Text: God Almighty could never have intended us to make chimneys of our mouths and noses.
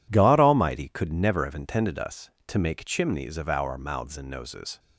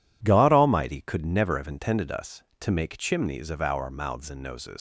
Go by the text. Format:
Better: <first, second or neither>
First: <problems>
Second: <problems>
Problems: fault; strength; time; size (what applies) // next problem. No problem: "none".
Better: first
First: none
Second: leaves "noses" unfinished; at 4.7 s; 115 ms